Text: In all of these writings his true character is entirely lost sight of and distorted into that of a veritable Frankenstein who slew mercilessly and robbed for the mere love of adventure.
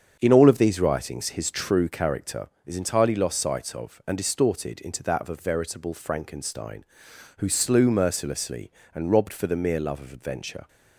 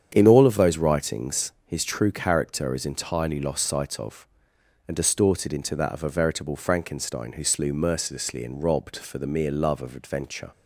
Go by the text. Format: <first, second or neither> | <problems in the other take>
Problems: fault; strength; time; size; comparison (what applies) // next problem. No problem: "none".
first | starts louder than the rest; strong; until 1.1 s; 8 dB; also in the first // says "those" for "these"; at 0.5 s